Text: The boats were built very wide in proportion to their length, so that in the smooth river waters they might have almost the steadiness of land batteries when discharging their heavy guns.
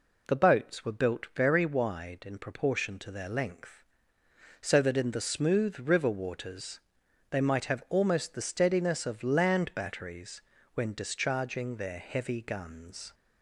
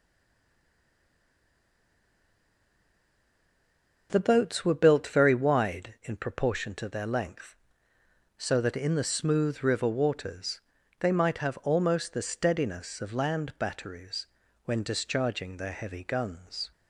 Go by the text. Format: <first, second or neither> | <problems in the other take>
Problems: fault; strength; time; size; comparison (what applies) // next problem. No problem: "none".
first | stays silent before the first word; strong; until 4.0 s; 4.0 s long // pauses between "waters" and "they"; at 10.5 s; 0.40 s long; noticeable in the first // pauses between "batteries" and "when"; at 14.2 s; 0.38 s long; slight in the first